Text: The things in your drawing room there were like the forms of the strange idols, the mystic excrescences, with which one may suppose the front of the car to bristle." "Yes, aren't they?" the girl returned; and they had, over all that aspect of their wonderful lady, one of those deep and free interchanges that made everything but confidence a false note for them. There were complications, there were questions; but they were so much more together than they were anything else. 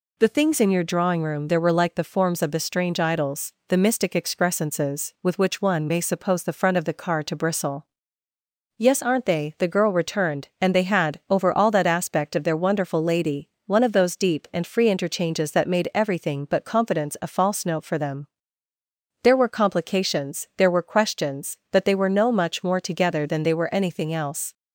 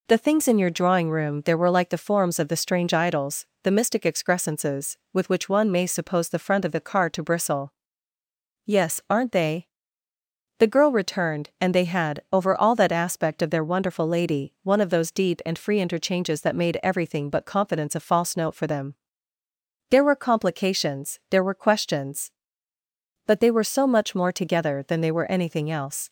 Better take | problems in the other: second | says "no" for "so"; at 22.0 s

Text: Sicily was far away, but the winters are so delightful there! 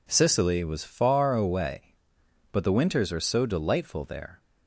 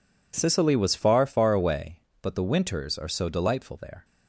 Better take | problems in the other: first | says "far" twice; at 1.2 s

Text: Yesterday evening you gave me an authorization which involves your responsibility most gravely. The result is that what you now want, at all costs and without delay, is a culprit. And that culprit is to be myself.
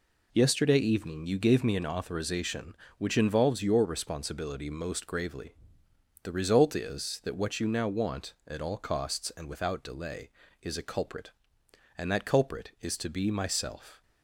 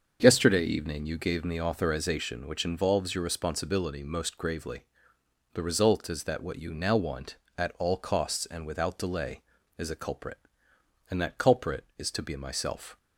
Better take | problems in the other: first | starts louder than the rest; until 1.2 s; 6.5 dB // skips "an"; at 1.5 s

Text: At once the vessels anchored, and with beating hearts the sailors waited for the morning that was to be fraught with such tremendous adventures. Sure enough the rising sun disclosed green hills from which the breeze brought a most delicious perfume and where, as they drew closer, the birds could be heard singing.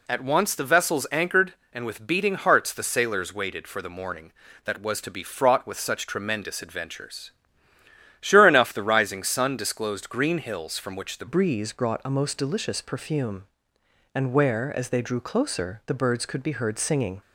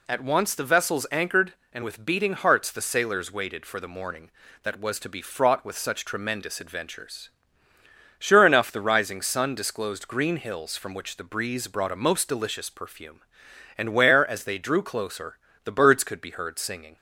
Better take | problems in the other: second | changes voice at "breeze"; from 11.2 s on; 6.0 s long

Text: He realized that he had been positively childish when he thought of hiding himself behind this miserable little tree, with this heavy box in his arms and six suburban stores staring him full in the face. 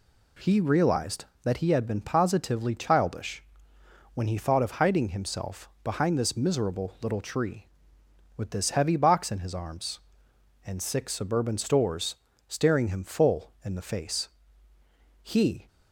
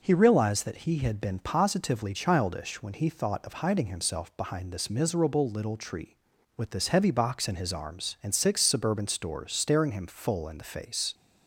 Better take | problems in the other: second | pauses between "childish" and "when"; noticeable; at 3.4 s; 0.70 s long // pauses between "stores" and "staring"; slight; at 12.1 s; 0.32 s long // goes on to say "He"; slight; from 15.2 s on; 0.46 s long

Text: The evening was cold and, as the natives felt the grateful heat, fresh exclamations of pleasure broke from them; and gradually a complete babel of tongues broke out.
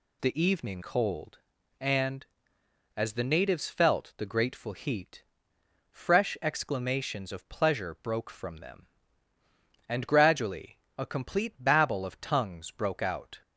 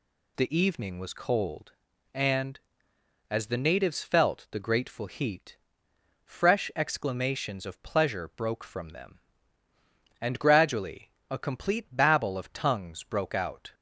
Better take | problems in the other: second | skips "was"; at 0.8 s // pauses between "gradually" and "a"; slight; at 10.7 s; 0.18 s long; slight in the second

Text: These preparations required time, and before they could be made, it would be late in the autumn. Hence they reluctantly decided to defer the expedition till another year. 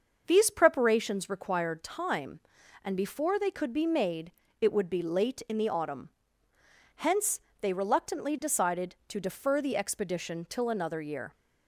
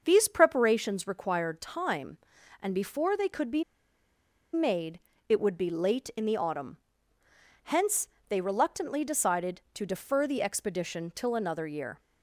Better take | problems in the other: first | starts louder than the rest; until 1.0 s; 6 dB; also in the first // pauses between "be" and "made"; noticeable; at 3.6 s; 0.90 s long // pauses between "Hence" and "they"; slight; at 8.0 s; 0.22 s long; slight in the first

